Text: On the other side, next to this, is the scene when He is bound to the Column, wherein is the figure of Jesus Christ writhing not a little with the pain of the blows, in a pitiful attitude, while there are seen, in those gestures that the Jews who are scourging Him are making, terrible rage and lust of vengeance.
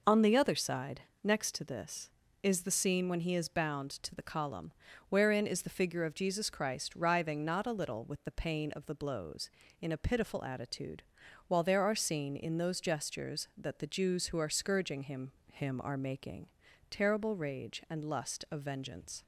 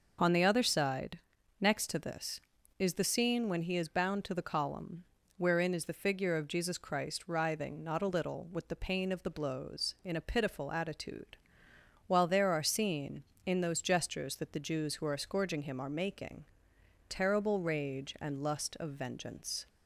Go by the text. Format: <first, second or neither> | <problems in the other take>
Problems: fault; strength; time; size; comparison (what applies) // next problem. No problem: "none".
second | says "Him" twice; at 15.5 s